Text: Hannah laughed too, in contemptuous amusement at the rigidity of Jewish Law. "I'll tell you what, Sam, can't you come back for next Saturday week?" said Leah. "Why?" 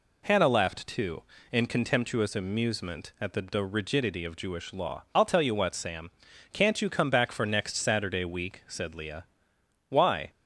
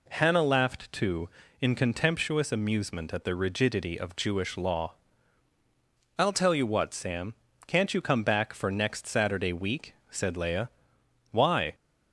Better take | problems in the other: second | says "the" twice; at 3.4 s

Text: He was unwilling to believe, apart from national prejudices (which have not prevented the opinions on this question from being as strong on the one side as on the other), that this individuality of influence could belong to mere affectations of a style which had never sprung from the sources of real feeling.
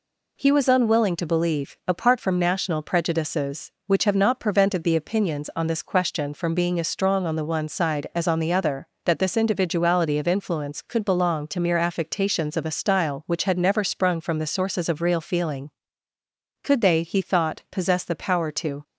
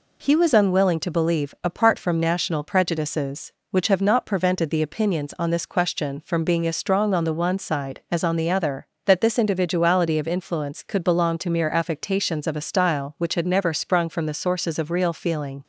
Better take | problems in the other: second | goes on to say "Could they he thought possess the power to"; strong; from 16.6 s on; 2.2 s long

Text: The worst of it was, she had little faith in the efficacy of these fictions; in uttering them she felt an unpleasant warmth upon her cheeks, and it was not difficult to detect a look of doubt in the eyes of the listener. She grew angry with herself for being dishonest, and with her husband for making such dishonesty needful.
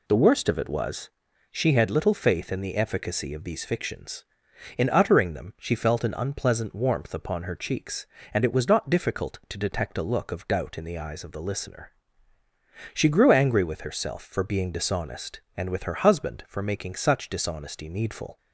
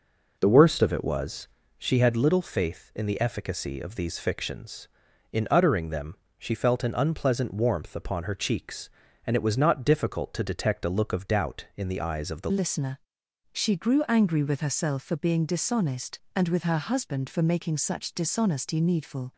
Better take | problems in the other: first | pauses between "them" and "she"; slight; at 6.1 s; 0.22 s long // changes voice at "listener"; from 12.5 s on; 6.8 s long

